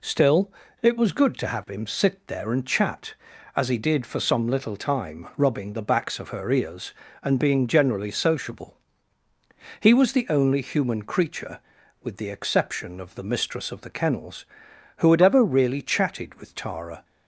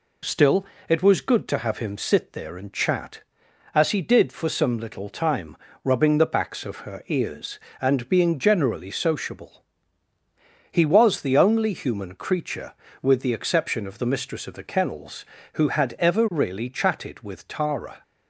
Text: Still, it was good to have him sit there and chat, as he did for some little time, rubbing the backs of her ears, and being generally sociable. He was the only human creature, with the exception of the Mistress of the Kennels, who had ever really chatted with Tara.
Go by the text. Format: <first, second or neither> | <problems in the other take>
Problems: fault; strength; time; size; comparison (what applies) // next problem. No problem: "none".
neither | none